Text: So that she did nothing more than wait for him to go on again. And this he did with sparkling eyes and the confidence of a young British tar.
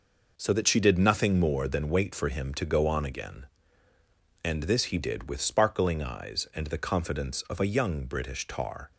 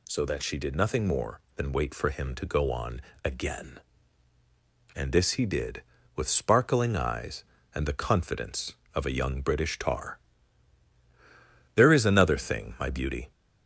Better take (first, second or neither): first